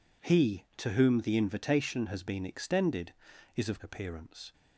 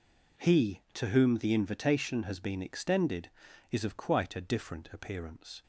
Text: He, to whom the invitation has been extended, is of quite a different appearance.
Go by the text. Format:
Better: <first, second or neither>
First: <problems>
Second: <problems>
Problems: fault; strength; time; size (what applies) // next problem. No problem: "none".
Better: second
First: skips "quite a different"; at 3.7 s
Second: none